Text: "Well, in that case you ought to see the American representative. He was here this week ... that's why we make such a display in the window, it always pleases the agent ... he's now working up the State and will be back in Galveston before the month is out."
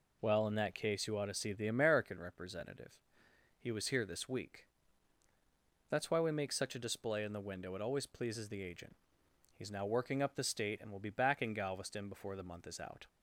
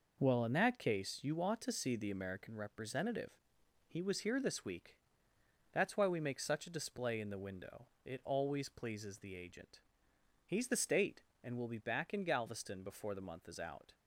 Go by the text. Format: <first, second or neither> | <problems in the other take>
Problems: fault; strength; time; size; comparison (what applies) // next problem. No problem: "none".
first | skips "now working up"; at 10.6 s